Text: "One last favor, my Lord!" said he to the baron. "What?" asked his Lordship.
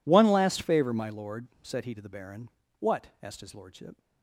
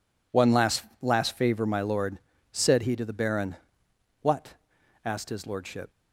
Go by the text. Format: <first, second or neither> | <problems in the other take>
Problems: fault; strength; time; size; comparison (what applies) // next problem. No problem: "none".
first | says "last" twice; at 1.0 s